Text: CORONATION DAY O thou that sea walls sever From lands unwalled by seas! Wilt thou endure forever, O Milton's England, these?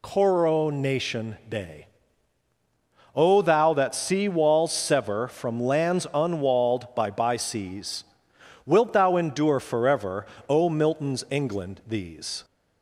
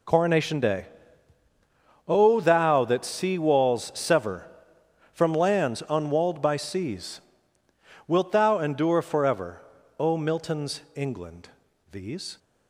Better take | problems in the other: second | pauses between "DAY" and "O"; strong; at 1.8 s; 1.2 s long; also in the second // says "by" twice; at 7.1 s

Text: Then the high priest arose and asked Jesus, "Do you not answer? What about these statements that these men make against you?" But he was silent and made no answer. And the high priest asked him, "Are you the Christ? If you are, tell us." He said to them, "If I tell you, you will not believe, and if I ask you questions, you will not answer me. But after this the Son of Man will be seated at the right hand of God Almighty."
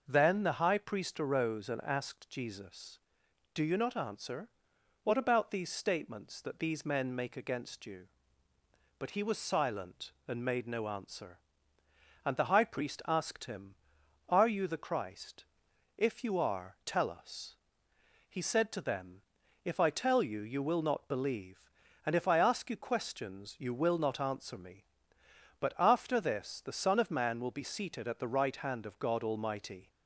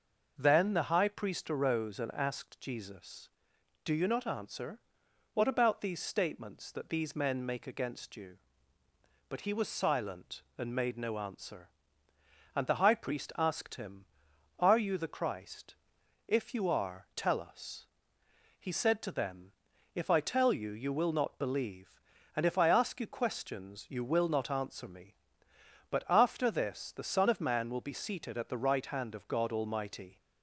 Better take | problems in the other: neither | none

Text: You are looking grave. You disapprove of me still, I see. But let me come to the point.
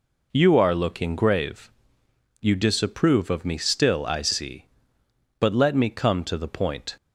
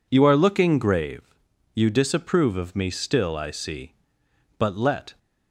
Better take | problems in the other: first | stops before "me come to the point"; at 5.1 s

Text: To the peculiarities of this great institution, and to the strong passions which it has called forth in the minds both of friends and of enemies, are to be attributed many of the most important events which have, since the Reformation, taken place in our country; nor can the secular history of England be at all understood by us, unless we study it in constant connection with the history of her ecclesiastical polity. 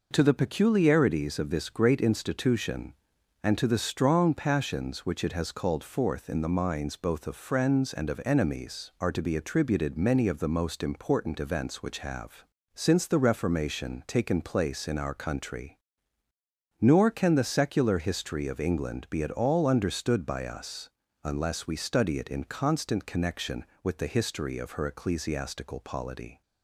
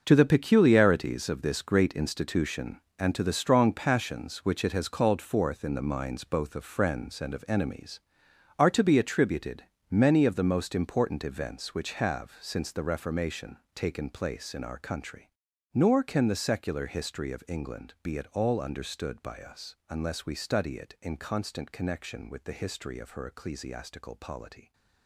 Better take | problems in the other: first | gets quieter; strong; throughout; 12 dB // pauses between "attributed" and "many"; slight; at 9.6 s; 0.26 s long

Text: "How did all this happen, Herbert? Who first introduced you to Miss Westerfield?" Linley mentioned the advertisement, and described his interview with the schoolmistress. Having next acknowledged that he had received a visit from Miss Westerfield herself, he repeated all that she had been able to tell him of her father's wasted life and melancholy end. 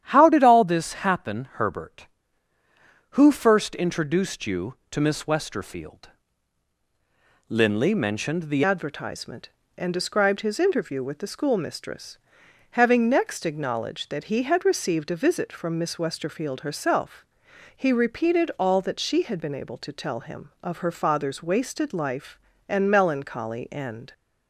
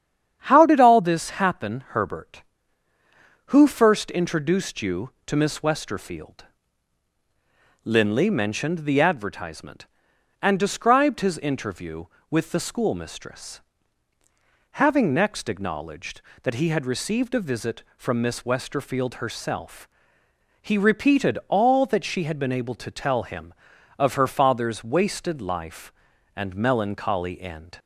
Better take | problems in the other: second | starts louder than the rest; strong; until 1.0 s; 10 dB; strong in the second // changes voice at "advertisement"; from 8.6 s on; 15.5 s long

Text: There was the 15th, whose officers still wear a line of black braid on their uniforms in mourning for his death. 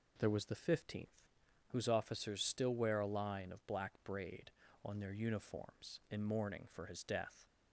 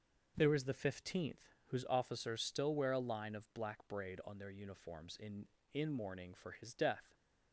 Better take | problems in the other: first | says "in" twice; at 5.7 s

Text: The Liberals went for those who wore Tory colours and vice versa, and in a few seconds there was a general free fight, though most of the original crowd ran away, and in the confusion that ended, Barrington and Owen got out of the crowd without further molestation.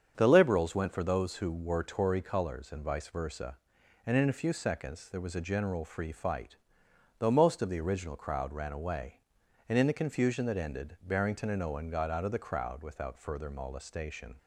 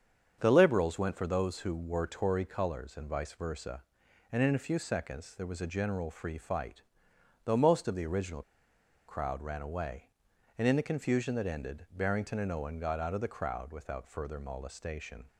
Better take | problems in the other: first | starts louder than the rest; strong; until 1.4 s; 7.5 dB; strong in the first // pauses between "original" and "crowd"; noticeable; at 8.4 s; 0.65 s long

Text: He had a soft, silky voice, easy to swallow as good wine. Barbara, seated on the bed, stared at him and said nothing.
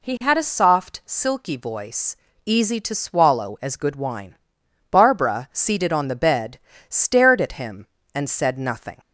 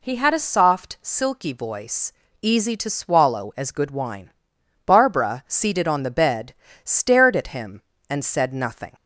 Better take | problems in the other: neither | none

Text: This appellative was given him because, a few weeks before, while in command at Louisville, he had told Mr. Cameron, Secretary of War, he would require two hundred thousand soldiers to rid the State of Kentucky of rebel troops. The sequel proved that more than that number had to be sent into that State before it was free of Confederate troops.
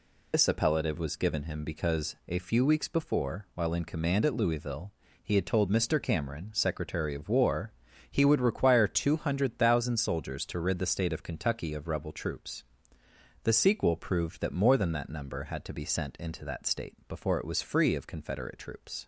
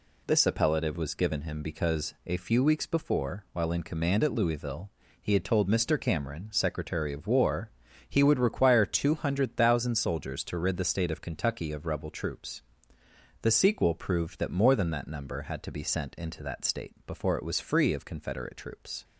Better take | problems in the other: second | loses the start of "This"; at 0.3 s; 65 ms

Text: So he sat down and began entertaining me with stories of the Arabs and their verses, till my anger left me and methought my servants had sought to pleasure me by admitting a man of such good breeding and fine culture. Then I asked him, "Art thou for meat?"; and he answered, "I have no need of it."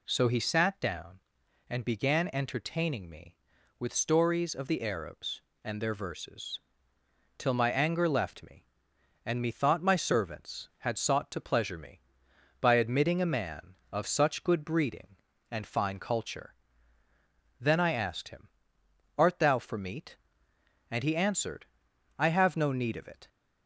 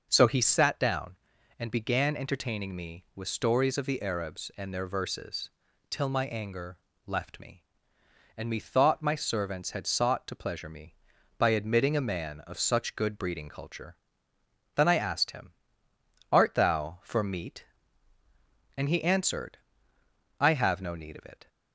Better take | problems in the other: first | pauses between "anger" and "left"; slight; at 6.7 s; 0.28 s long // skips "and fine"; at 13.5 s

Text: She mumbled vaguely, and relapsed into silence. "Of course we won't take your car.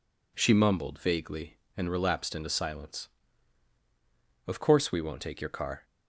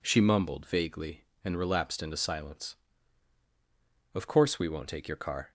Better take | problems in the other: neither | none

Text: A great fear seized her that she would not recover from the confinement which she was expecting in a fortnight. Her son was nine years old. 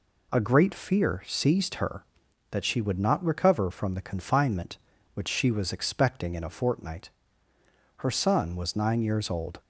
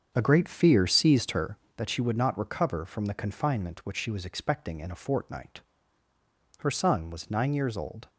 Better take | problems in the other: first | starts louder than the rest; strong; until 1.9 s; 7 dB

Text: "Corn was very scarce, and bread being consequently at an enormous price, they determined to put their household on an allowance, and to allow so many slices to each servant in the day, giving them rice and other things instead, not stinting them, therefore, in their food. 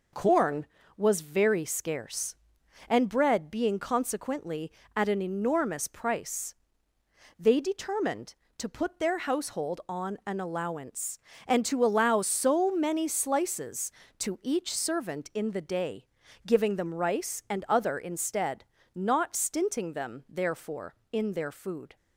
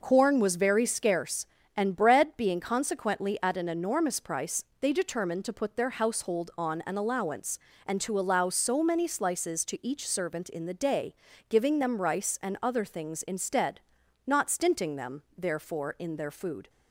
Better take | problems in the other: second | skips "things"; at 17.9 s

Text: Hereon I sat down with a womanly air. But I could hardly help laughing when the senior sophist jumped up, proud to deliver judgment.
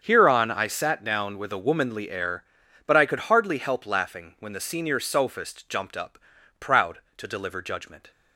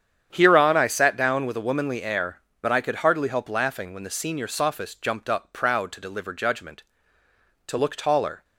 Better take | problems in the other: first | starts louder than the rest; strong; until 1.3 s; 8.5 dB; strong in the first // goes on to say "To look taller"; noticeable; from 7.6 s on; 0.76 s long

